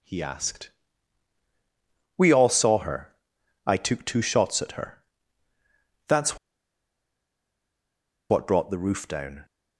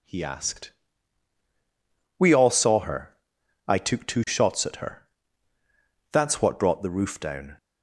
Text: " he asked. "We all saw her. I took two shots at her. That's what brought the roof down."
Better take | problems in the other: second | pauses between "That's" and "what"; strong; at 6.3 s; 1.9 s long

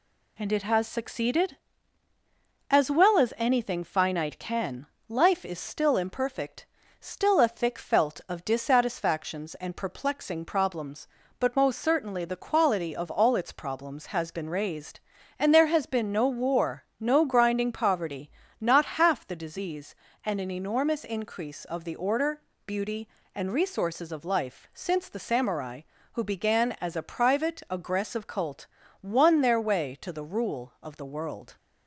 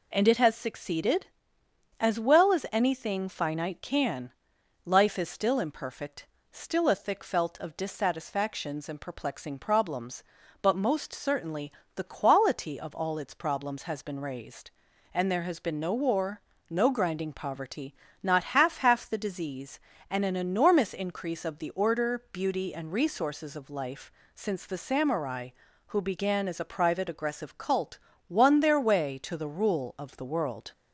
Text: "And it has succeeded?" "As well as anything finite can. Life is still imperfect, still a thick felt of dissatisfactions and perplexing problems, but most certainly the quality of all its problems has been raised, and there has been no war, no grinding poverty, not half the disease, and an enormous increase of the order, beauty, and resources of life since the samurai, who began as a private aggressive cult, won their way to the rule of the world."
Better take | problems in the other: first | pauses between "certainly" and "the"; slight; at 11.7 s; 0.24 s long // says "half" twice; at 18.7 s // pauses between "life" and "since"; slight; at 24.1 s; 0.24 s long

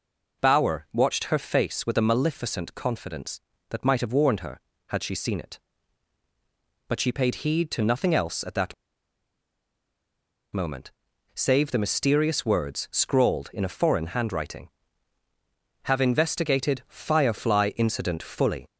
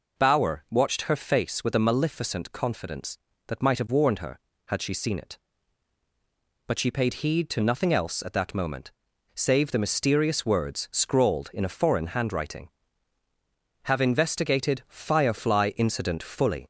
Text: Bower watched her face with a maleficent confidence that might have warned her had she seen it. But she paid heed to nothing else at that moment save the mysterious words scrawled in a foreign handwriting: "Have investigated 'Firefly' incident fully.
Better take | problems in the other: second | pauses between "that" and "moment"; strong; at 8.7 s; 1.7 s long // pauses between "moment" and "save"; noticeable; at 10.9 s; 0.46 s long; noticeable in the second

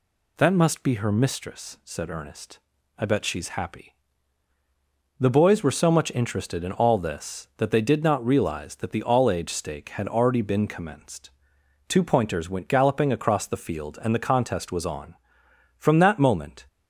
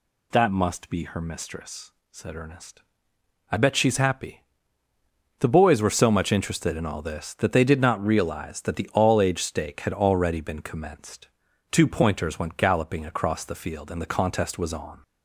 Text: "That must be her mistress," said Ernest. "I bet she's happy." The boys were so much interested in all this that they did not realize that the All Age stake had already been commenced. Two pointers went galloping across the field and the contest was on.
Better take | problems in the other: second | goes on to say "From that moment"; noticeable; from 15.7 s on; 0.88 s long

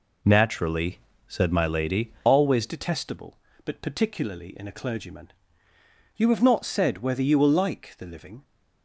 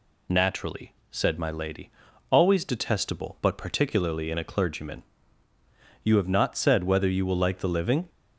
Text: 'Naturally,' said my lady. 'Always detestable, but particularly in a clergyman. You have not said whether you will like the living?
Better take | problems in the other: second | changes voice at "detestable"; from 2.6 s on; 5.8 s long

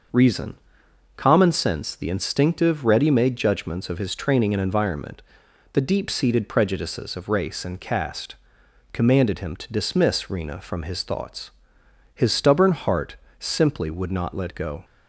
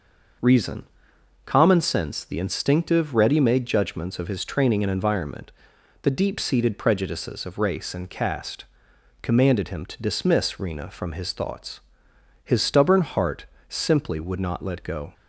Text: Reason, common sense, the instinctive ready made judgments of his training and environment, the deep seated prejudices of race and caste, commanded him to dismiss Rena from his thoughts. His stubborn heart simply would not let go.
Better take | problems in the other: neither | starts louder than the rest; noticeable; the same in both // pauses between "heart" and "simply"; slight; the same in both

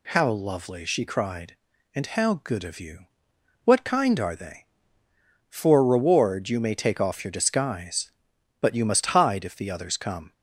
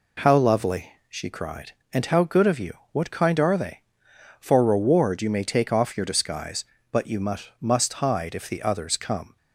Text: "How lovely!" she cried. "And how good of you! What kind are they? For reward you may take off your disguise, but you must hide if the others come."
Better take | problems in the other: first | says "must" twice; at 7.6 s

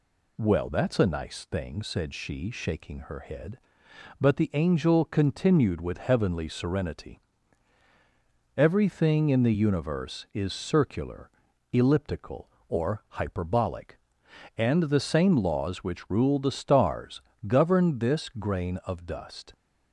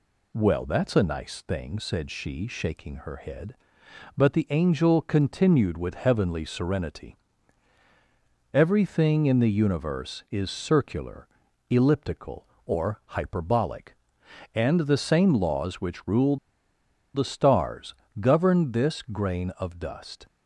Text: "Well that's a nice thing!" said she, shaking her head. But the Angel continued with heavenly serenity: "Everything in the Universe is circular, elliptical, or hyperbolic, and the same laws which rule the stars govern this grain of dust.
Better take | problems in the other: first | pauses between "rule" and "the"; noticeable; at 16.3 s; 0.78 s long // pauses between "stars" and "govern"; slight; at 17.9 s; 0.26 s long; slight in the first

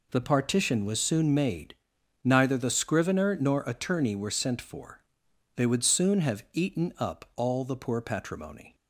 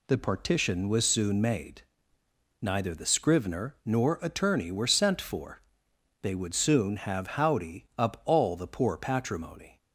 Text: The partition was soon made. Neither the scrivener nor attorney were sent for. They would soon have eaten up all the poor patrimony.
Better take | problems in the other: first | says "howdy" for "eaten"; at 7.3 s

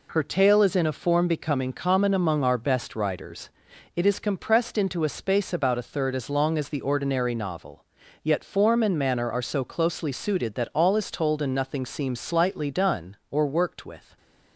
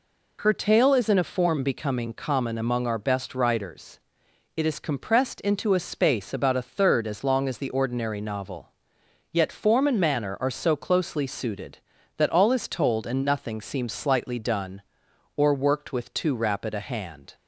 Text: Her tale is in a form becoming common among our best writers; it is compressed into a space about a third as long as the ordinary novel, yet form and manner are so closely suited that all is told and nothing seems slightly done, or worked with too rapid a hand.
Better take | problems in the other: second | stops before "too rapid a hand"; at 14.1 s

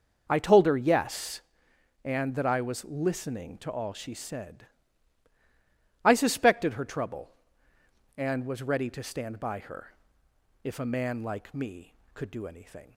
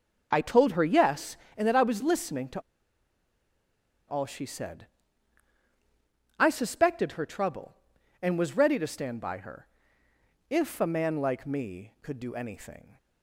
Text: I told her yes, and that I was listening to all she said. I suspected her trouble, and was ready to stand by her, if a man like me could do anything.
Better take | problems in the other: first | starts louder than the rest; until 1.3 s; 7 dB; noticeable in the first // pauses between "to" and "all"; strong; at 2.5 s; 1.4 s long

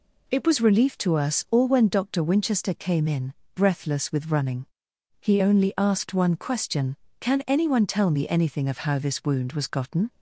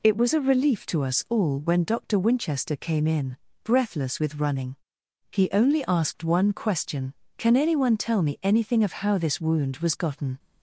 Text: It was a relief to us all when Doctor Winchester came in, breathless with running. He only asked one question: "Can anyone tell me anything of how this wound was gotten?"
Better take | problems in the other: second | skips "a"; at 0.5 s

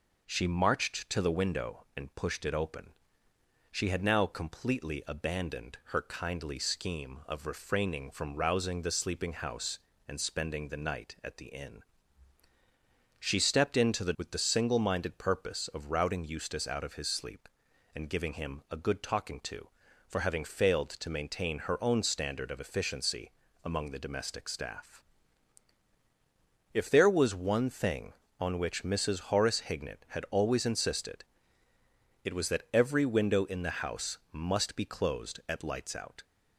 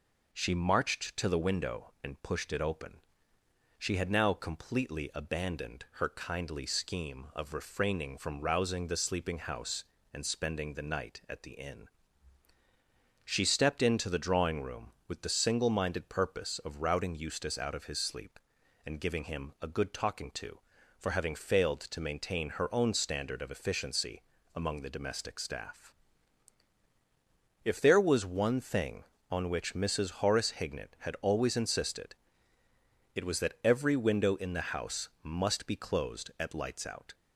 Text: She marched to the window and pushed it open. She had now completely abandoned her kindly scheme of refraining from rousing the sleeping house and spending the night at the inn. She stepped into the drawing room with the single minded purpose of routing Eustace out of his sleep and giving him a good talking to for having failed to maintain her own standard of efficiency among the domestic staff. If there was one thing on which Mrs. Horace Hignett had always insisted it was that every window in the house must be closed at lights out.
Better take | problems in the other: second | skips "drawing room"; at 14.1 s // pauses between "efficiency" and "among"; slight; at 23.3 s; 0.34 s long; slight in the second // pauses between "insisted" and "it"; noticeable; at 31.2 s; 0.98 s long; noticeable in the second // pauses between "house" and "must"; slight; at 34.1 s; 0.16 s long; slight in the second

